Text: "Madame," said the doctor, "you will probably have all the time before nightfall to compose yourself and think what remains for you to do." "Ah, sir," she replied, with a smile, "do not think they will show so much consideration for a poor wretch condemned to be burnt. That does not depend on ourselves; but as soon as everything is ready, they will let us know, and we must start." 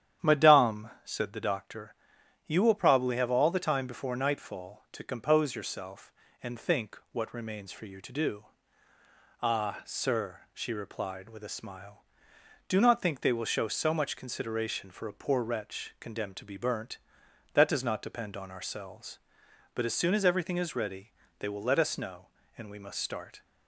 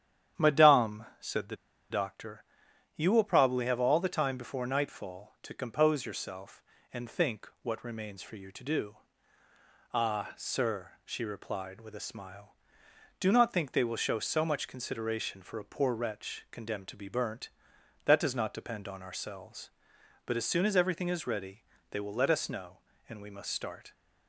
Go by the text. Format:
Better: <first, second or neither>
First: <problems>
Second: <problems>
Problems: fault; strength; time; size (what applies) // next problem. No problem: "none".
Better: first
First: starts louder than the rest; strong; until 1.3 s; 10 dB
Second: starts louder than the rest; strong; until 1.5 s; 10 dB // pauses between "the" and "doctor"; slight; at 1.5 s; 0.34 s long